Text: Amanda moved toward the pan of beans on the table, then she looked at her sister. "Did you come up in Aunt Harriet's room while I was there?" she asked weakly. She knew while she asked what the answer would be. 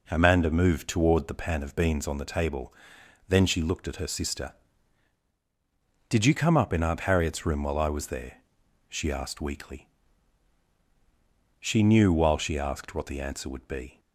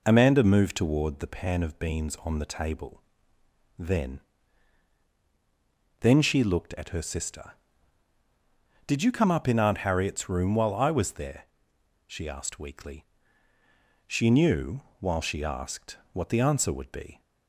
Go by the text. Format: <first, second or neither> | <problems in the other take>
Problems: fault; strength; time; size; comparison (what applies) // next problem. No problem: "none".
first | says "then" twice; at 6.0 s // pauses between "knew" and "while"; slight; at 14.8 s; 0.18 s long